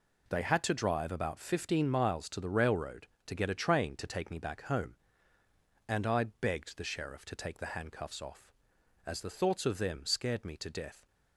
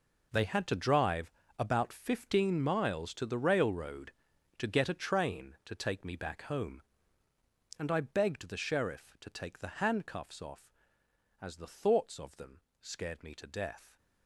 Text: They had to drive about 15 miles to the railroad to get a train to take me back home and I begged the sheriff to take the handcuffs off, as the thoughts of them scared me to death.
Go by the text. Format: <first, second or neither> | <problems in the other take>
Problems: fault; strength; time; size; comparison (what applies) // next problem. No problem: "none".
first | gets quieter; strong; throughout; 13.5 dB // pauses between "drive" and "about"; slight; at 1.3 s; 0.26 s long // pauses between "them" and "scared"; slight; at 12.5 s; 0.22 s long